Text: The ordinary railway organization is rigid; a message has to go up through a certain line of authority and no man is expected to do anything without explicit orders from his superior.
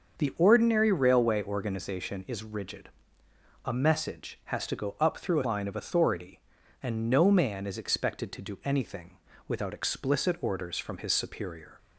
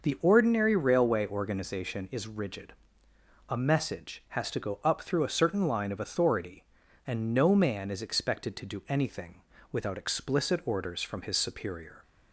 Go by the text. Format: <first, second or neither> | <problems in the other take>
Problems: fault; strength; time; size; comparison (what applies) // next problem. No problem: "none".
second | starts louder than the rest; until 1.2 s; 6.5 dB // skips "certain"; at 5.4 s // pauses between "anything" and "without"; slight; at 9.1 s; 0.30 s long; slight in the second